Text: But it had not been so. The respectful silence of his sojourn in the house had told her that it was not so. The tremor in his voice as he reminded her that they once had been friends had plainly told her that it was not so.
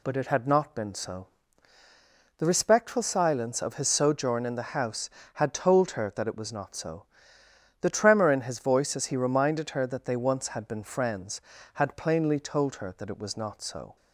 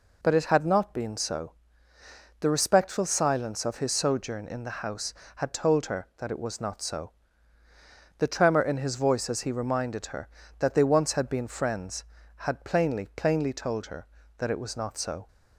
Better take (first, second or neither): first